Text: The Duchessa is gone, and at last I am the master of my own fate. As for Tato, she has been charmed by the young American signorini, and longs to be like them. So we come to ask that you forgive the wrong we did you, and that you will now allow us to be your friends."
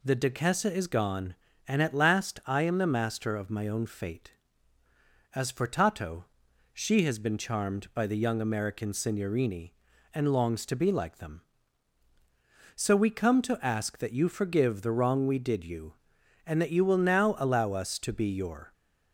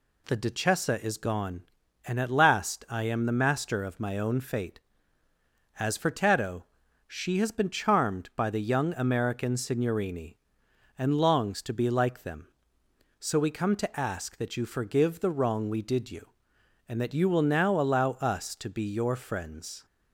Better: second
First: stops before "friends"; at 18.7 s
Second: none

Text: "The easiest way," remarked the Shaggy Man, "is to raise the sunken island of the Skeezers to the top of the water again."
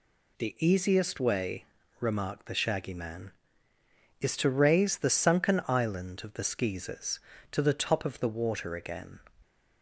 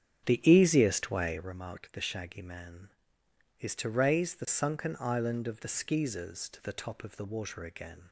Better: first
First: none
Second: starts louder than the rest; strong; until 1.5 s; 9 dB

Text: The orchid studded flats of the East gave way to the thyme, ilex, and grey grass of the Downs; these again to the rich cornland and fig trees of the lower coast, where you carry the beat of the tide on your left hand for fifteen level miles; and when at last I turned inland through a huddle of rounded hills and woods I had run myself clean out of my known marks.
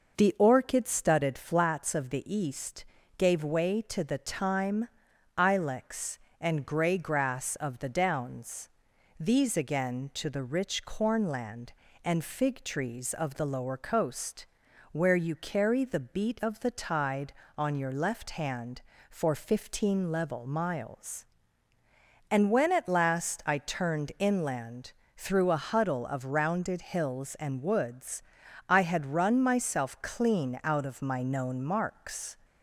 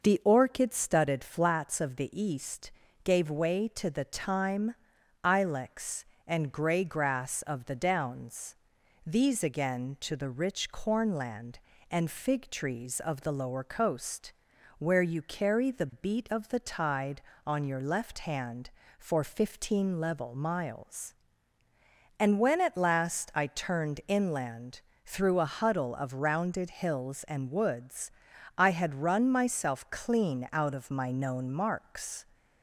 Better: neither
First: pauses between "East" and "gave"; slight; at 2.8 s; 0.32 s long // pauses between "inland" and "through"; slight; at 24.9 s; 0.24 s long // pauses between "woods" and "I"; at 28.2 s; 0.44 s long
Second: pauses between "East" and "gave"; slight; at 2.7 s; 0.32 s long // pauses between "inland" and "through"; slight; at 24.8 s; 0.24 s long // pauses between "woods" and "I"; at 28.1 s; 0.44 s long

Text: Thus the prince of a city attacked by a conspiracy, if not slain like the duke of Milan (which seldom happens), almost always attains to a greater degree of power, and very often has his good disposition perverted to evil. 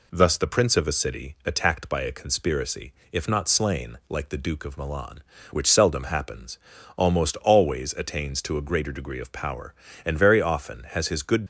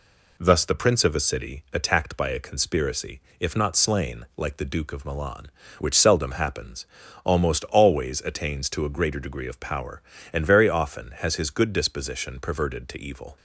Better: second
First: stops before "disposition perverted to evil"; at 11.4 s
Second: none

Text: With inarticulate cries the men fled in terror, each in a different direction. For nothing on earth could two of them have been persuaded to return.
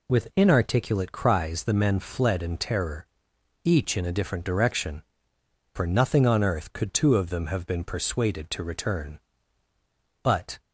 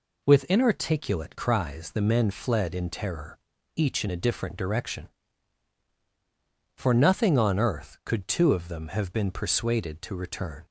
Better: second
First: goes on to say "But"; slight; from 10.2 s on; 0.38 s long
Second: none

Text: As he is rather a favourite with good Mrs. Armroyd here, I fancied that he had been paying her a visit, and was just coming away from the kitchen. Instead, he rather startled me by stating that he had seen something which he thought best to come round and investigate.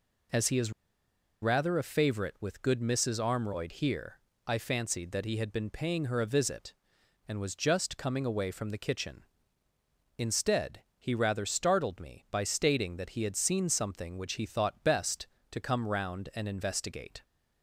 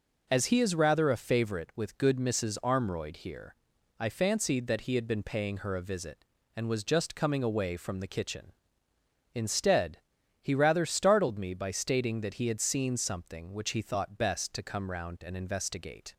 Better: second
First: pauses between "is" and "rather"; noticeable; at 0.7 s; 0.70 s long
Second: none

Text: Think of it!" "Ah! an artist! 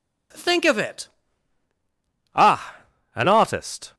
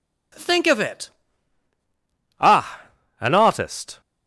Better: neither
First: none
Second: none

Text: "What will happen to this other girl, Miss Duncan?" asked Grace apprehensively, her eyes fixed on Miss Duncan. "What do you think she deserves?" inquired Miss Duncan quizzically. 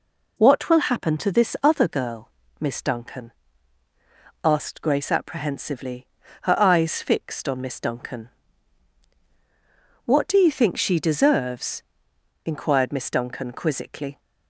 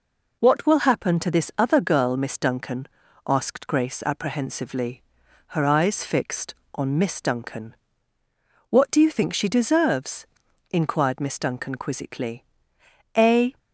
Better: first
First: none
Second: goes on to say "A"; slight; from 13.1 s on; 0.42 s long

